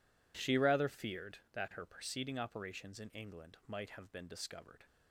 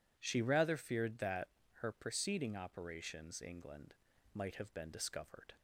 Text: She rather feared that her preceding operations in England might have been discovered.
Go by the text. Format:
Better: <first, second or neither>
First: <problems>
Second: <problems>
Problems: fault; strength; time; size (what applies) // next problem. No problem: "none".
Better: first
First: none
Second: pauses between "that" and "her"; slight; at 1.4 s; 0.32 s long // skips "in"; at 3.4 s // pauses between "England" and "might"; at 3.9 s; 0.40 s long